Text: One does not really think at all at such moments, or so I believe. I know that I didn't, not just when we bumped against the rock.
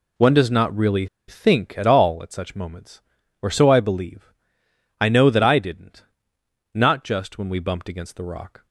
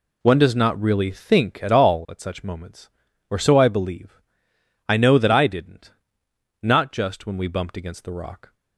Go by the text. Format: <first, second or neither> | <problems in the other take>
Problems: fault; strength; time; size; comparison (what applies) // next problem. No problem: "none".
second | pauses between "really" and "think"; slight; at 1.0 s; 0.22 s long